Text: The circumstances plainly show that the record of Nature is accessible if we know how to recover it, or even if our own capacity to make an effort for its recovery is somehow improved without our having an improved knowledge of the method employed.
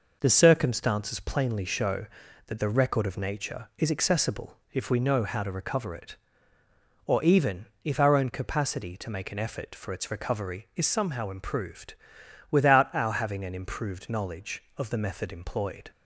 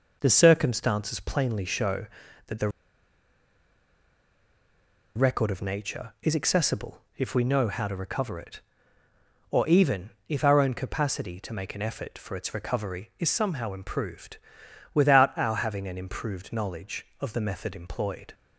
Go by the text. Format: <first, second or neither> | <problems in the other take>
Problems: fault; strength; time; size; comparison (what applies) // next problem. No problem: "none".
first | pauses between "the" and "record"; strong; at 2.6 s; 2.4 s long // pauses between "accessible" and "if"; slight; at 6.9 s; 0.16 s long; slight in the first // pauses between "even" and "if"; slight; at 10.0 s; 0.18 s long; slight in the first // pauses between "improved" and "without"; noticeable; at 14.3 s; 0.56 s long; noticeable in the first